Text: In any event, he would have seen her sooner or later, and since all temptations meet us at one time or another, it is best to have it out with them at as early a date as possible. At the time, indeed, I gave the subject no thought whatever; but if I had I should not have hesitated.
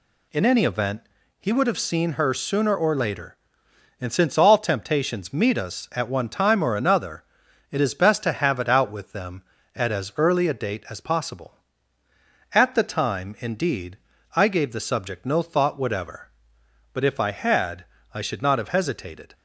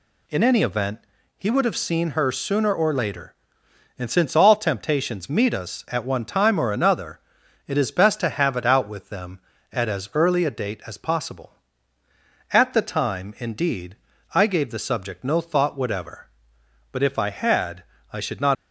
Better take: first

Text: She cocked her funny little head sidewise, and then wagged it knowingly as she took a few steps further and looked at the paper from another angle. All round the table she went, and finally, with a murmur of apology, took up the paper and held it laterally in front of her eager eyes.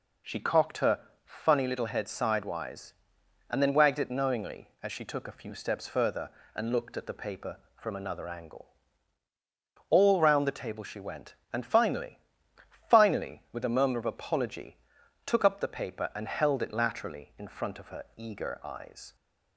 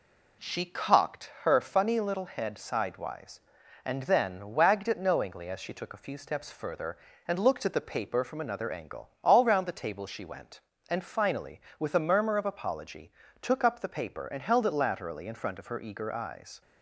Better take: second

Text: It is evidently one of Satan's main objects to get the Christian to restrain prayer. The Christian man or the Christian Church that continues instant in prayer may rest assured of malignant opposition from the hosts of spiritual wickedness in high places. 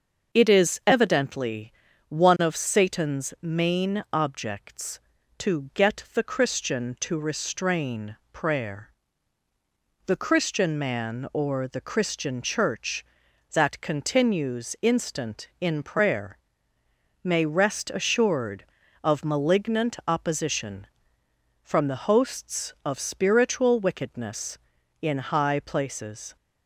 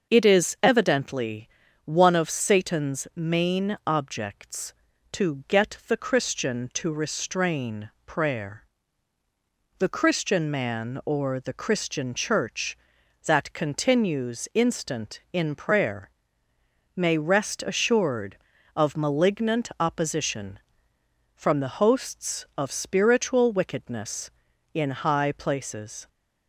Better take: neither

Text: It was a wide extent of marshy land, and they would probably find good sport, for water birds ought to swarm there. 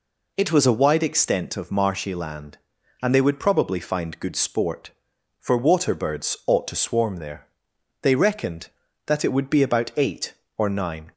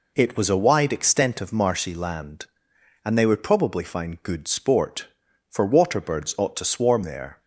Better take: second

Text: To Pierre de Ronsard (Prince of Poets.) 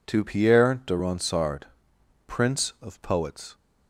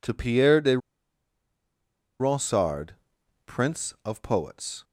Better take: first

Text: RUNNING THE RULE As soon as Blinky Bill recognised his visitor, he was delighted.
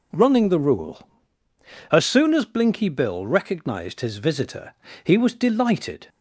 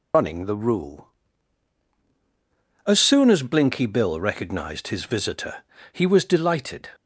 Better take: first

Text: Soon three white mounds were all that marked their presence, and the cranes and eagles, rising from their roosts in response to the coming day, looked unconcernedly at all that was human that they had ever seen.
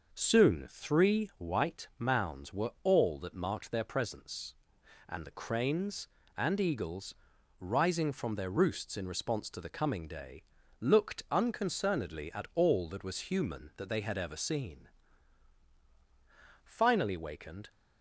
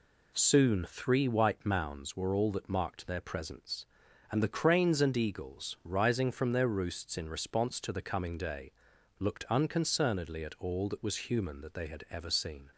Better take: second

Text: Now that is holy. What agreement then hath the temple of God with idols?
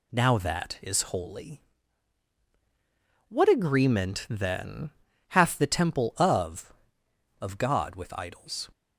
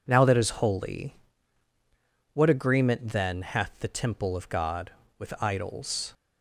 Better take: second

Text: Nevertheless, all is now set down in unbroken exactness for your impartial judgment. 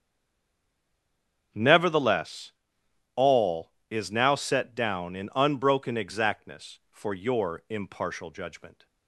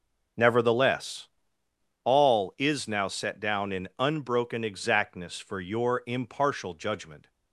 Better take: second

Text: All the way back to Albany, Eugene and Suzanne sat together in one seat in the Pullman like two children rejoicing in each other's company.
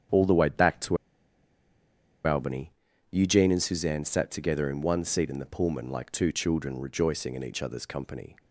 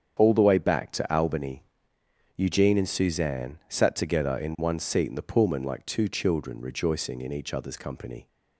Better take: second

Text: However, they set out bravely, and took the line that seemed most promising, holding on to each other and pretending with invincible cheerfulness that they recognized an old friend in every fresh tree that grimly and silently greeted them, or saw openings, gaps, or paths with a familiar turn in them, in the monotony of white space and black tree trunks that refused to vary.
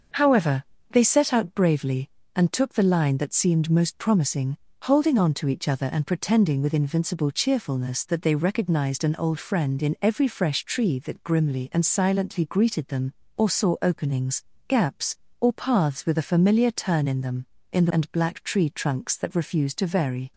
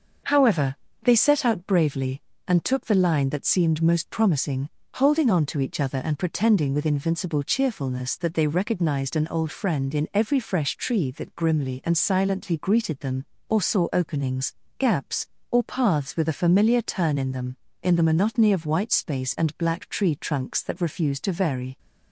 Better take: second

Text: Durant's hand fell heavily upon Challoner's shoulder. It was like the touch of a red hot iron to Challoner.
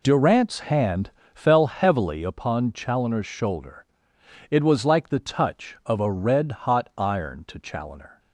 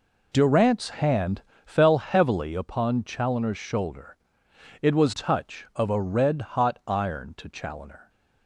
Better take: first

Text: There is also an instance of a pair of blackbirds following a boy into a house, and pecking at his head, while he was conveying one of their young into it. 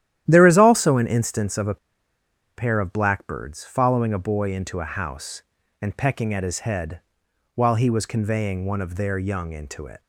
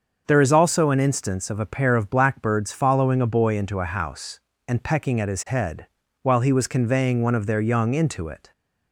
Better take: second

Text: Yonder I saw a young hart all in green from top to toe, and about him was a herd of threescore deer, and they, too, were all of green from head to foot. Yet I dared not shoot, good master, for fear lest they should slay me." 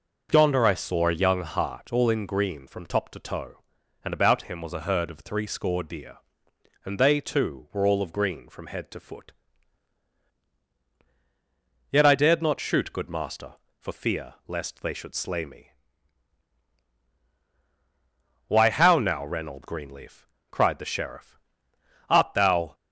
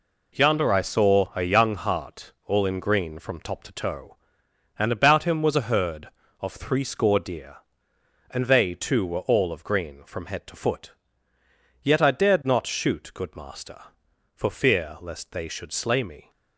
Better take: second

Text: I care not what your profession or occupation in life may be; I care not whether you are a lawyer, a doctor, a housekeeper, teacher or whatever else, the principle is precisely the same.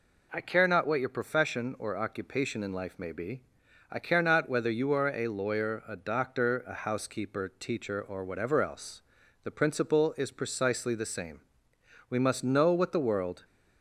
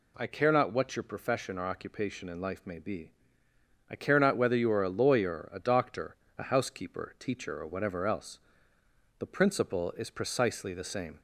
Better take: second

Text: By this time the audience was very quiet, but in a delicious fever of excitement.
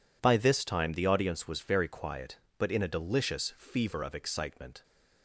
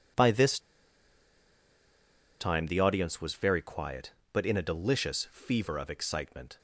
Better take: first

